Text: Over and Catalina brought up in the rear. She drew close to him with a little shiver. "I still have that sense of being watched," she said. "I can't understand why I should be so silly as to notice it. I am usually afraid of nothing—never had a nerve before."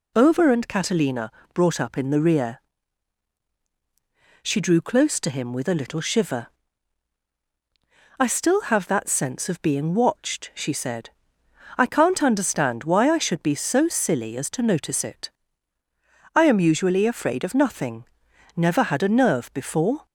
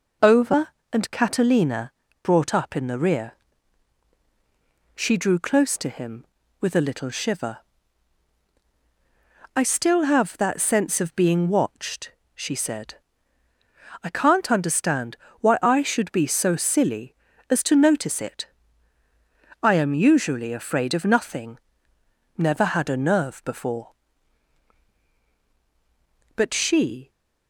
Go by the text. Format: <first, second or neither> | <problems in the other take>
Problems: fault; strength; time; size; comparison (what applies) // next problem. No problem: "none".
first | pauses between "Catalina" and "brought"; slight; at 1.9 s; 0.32 s long; slight in the first // pauses between "understand" and "why"; slight; at 15.1 s; 0.24 s long // goes on to say "But she"; noticeable; from 26.3 s on; 0.74 s long